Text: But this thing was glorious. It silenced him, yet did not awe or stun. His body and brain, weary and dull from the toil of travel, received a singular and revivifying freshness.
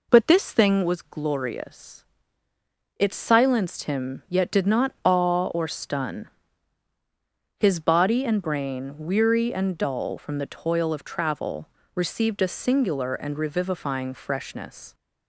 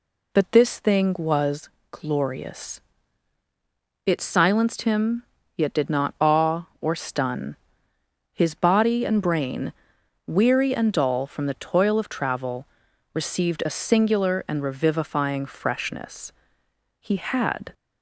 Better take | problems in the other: first | pauses between "was" and "glorious"; slight; at 1.6 s; 0.24 s long // goes on to say "He had"; noticeable; from 17.0 s on; 0.72 s long

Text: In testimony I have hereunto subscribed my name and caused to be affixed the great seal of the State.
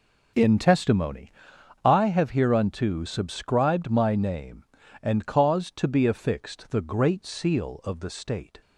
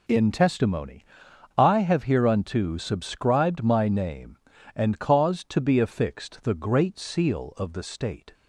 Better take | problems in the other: second | starts louder than the rest; noticeable; until 1.6 s; 5 dB // pauses between "testimony" and "I"; noticeable; at 1.3 s; 0.54 s long; noticeable in the second

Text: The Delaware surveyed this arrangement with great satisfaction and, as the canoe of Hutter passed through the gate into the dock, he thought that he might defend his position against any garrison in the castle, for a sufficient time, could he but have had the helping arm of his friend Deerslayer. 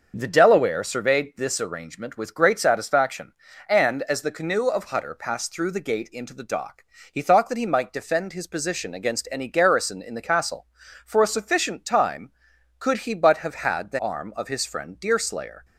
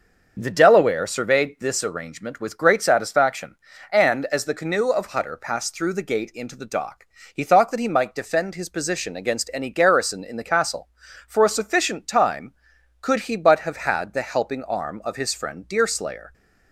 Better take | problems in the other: second | starts louder than the rest; noticeable; until 1.1 s; 6 dB; noticeable in the second // skips "helping"; at 13.9 s

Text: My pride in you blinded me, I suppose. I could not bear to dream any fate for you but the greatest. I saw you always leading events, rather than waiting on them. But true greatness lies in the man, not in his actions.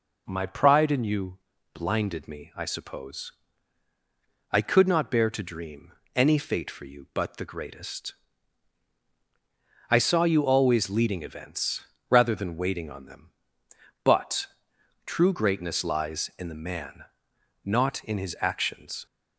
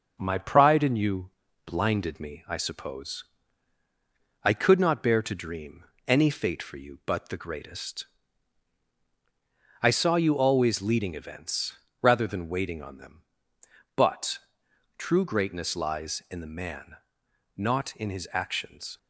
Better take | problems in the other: first | gets quieter; slight; throughout; 3 dB // pauses between "you" and "blinded"; slight; at 1.2 s; 0.36 s long; slight in the first // pauses between "dream" and "any"; slight; at 5.8 s; 0.24 s long; slight in the first // pauses between "But" and "true"; noticeable; at 14.3 s; 0.58 s long; noticeable in the first

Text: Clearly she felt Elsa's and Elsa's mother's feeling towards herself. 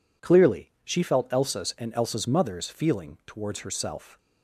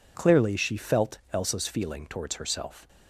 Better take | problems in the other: first | pauses between "felt" and "Elsa's"; slight; at 1.1 s; 0.16 s long // skips "and Elsa's mother's"; at 1.6 s

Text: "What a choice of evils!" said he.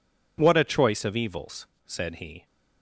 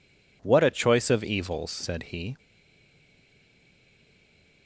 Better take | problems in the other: first | stays silent after the last word; from 2.3 s on; 2.3 s long

